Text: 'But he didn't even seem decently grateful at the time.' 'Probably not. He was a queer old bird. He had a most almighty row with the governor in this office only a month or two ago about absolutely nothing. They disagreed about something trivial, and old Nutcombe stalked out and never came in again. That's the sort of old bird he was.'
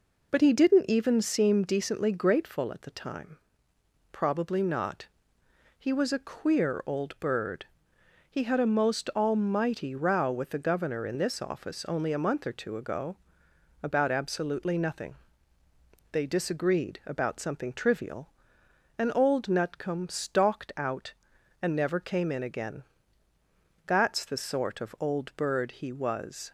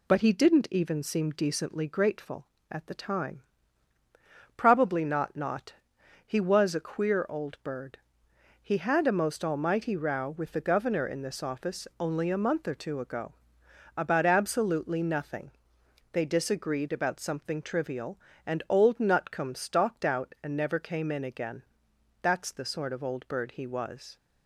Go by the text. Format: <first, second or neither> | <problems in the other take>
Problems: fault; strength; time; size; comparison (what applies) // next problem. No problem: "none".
first | says "not" twice; at 5.3 s // pauses between "ago" and "about"; noticeable; at 13.3 s; 0.64 s long; noticeable in the first